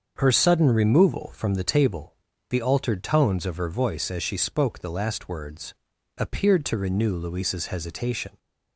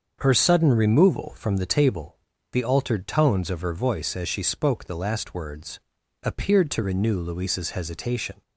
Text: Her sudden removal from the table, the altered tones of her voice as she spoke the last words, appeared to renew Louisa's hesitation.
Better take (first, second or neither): neither